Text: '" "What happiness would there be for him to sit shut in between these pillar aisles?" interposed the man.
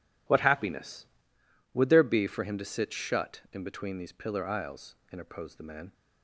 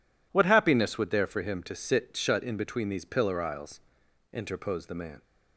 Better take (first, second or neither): first